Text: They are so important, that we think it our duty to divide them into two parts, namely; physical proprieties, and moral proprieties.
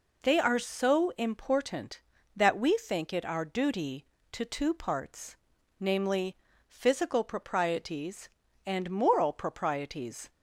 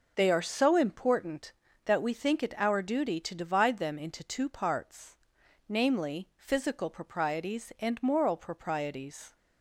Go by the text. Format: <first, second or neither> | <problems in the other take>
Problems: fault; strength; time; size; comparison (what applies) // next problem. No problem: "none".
second | skips "divide them into"; at 4.4 s